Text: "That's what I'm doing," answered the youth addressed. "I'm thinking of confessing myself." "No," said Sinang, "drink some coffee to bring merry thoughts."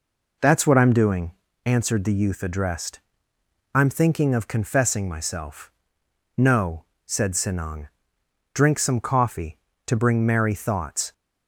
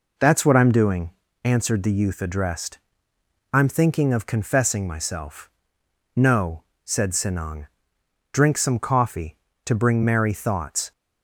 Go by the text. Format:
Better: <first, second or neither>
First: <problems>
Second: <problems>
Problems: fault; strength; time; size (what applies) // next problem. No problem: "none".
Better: neither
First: none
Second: none